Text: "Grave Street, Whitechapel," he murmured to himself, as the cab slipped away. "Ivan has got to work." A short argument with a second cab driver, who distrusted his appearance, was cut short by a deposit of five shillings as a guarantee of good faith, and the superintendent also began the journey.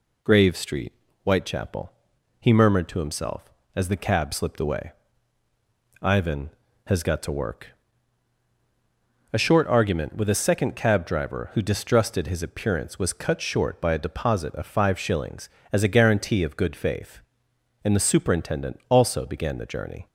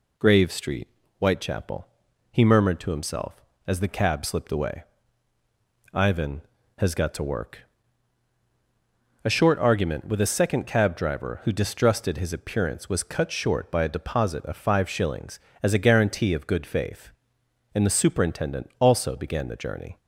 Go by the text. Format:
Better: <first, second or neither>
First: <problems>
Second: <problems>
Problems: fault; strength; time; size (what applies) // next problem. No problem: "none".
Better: neither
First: none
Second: none